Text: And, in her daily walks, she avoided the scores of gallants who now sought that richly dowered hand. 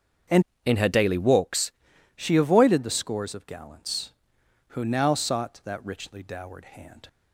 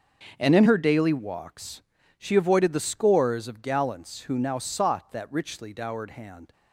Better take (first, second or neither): second